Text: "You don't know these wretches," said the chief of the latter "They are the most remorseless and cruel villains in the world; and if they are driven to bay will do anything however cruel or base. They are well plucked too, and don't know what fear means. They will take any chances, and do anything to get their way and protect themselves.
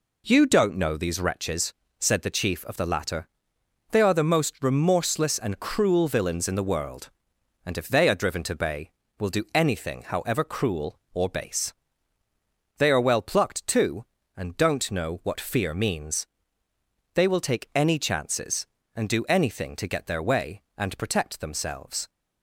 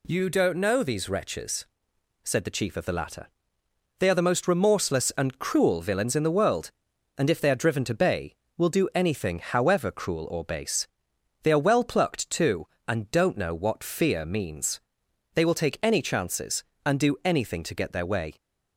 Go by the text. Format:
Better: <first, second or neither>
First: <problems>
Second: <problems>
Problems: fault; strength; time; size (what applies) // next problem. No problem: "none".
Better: first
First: pauses between "latter" and "They"; noticeable; at 3.2 s; 0.64 s long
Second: pauses between "latter" and "They"; noticeable; at 3.2 s; 0.70 s long // stops before "and protect themselves"; at 18.3 s